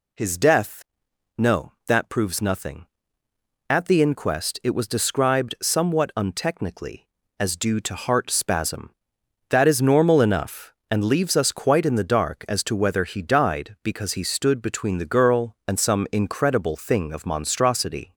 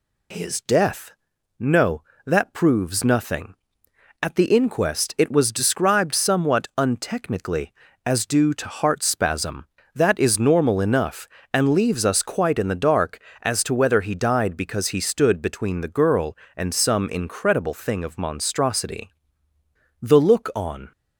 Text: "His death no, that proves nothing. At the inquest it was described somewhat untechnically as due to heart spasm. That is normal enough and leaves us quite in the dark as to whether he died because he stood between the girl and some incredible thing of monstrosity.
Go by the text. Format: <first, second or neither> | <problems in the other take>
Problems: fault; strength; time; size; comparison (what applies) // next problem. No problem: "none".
first | pauses between "death" and "no"; noticeable; at 1.1 s; 0.48 s long; noticeable in the first // goes on to say "The look on"; noticeable; from 20.0 s on; 0.90 s long